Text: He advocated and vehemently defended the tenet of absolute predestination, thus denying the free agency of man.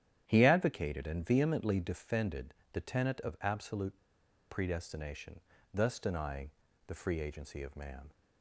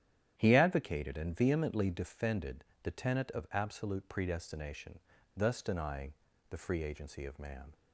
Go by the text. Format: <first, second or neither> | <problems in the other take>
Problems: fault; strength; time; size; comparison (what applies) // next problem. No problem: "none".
second | starts louder than the rest; strong; until 1.2 s; 10.5 dB; strong in the second // pauses between "defended" and "the"; slight; at 2.5 s; 0.20 s long; slight in the second // pauses between "absolute" and "predestination"; noticeable; at 3.9 s; 0.54 s long // pauses between "denying" and "the"; slight; at 6.5 s; 0.34 s long; slight in the second